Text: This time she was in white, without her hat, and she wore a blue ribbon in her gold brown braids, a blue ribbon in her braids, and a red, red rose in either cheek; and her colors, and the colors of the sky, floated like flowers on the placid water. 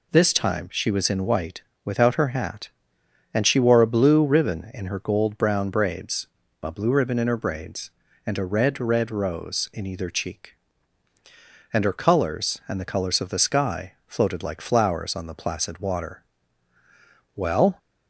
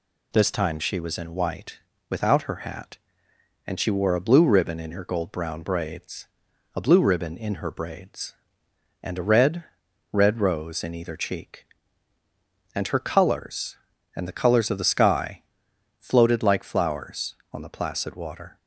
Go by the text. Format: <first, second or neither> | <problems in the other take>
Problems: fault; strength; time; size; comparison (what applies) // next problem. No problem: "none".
second | goes on to say "Well"; slight; from 17.3 s on; 0.42 s long